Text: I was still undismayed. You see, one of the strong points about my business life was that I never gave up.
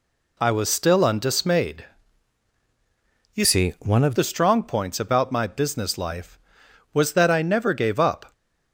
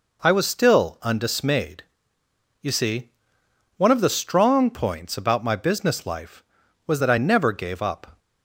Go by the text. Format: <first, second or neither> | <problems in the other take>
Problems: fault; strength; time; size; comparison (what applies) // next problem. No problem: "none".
second | changes voice from "see" to "of"; from 3.4 to 4.1 s; 0.7 s long